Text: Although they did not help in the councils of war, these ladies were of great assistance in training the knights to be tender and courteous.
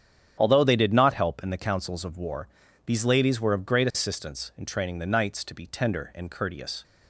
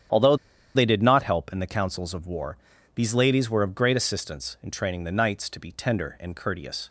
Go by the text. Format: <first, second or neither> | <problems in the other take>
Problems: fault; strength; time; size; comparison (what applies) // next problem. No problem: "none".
first | starts louder than the rest; strong; until 1.5 s; 9.5 dB; strong in the first // pauses between "Although" and "they"; at 0.3 s; 0.40 s long